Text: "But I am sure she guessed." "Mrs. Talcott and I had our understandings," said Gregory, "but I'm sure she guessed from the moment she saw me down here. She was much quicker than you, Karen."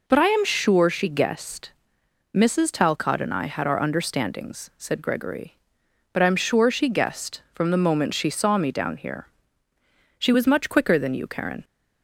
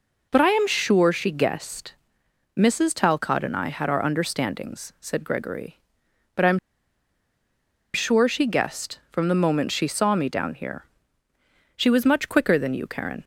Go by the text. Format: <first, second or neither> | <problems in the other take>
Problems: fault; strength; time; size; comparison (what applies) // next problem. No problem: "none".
first | pauses between "I'm" and "sure"; strong; at 6.5 s; 1.3 s long